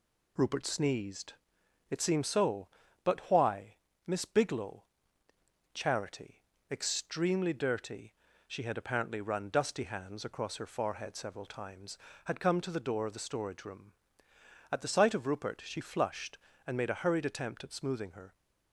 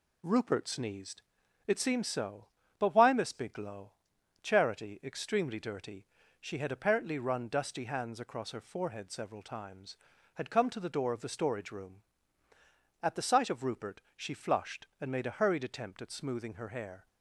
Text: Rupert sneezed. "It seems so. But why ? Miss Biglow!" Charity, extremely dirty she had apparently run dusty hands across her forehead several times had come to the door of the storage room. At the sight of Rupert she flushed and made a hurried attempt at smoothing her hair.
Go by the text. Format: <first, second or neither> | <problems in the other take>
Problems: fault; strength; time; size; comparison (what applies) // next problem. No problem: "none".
second | pauses between "dirty" and "she"; slight; at 8.1 s; 0.34 s long; slight in the second // stops before "hair"; at 18.3 s